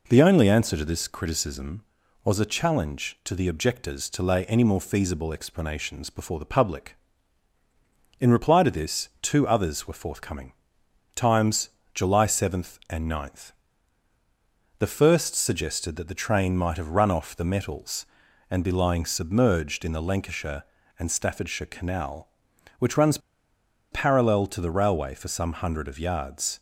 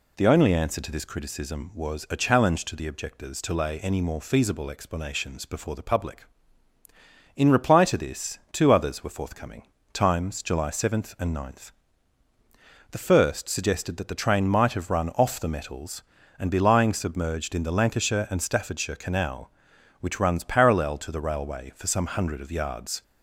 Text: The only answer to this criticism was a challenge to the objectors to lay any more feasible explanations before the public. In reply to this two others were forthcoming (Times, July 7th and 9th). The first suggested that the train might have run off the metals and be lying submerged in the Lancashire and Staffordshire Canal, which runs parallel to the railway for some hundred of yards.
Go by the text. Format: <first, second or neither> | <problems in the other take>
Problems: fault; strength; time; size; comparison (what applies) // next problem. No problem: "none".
second | pauses between "runs" and "parallel"; noticeable; at 23.1 s; 0.73 s long